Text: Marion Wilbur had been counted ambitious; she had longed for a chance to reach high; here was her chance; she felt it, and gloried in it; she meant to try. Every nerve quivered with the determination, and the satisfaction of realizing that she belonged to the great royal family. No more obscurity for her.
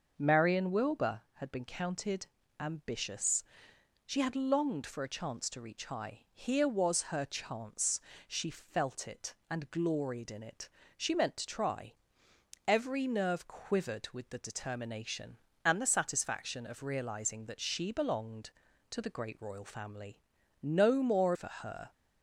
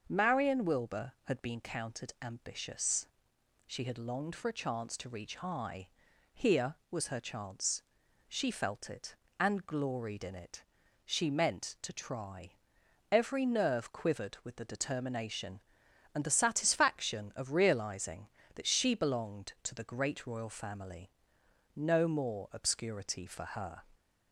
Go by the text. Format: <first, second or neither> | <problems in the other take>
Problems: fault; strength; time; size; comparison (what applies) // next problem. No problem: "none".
second | starts louder than the rest; until 1.1 s; 6 dB; also in the second // pauses between "counted" and "ambitious"; slight; at 2.2 s; 0.30 s long // skips "obscurity"; at 21.3 s